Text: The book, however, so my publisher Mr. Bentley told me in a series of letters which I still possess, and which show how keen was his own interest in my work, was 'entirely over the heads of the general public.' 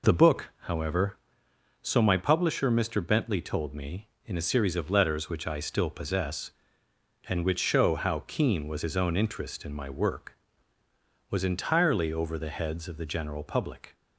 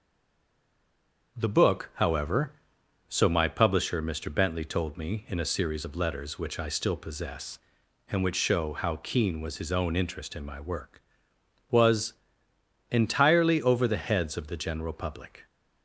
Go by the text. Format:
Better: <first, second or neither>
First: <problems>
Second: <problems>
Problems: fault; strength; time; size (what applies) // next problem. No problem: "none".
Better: first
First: none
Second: stays silent before the first word; noticeable; until 1.3 s; 1.3 s long // starts louder than the rest; until 2.4 s; 6.5 dB // pauses between "was" and "entirely"; noticeable; at 12.1 s; 0.78 s long